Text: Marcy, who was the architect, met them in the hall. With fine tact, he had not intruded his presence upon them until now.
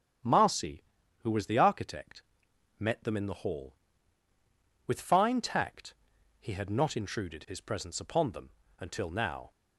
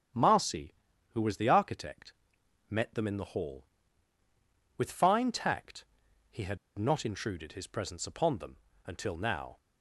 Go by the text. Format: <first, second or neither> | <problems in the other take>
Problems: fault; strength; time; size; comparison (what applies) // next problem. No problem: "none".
first | starts louder than the rest; strong; until 1.5 s; 8.5 dB; strong in the first // pauses between "had" and "not"; slight; at 6.5 s; 0.21 s long // pauses between "them" and "until"; slight; at 8.5 s; 0.28 s long; slight in the first